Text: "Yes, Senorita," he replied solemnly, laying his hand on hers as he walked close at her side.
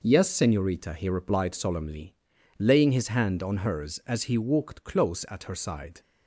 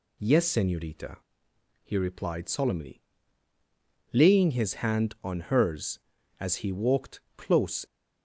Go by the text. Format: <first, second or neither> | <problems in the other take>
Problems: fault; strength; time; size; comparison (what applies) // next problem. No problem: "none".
first | pauses between "walked" and "close"; slight; at 7.1 s; 0.18 s long // stops before "at her side"; at 7.8 s